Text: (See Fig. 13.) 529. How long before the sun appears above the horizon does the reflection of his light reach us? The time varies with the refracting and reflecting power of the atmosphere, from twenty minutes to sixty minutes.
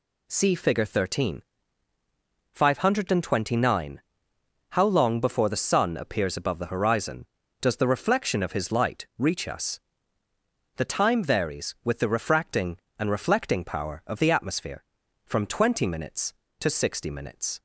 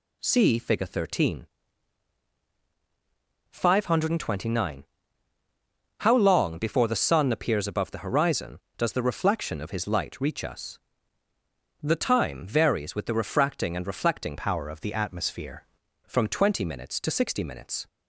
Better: first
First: none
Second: changes voice from "power" to "atmosphere"; from 14.3 to 15.6 s; 1.3 s long

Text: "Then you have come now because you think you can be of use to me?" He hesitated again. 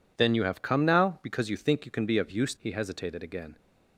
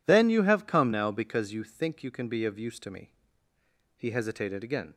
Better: second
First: skips "to me"; at 2.5 s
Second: none

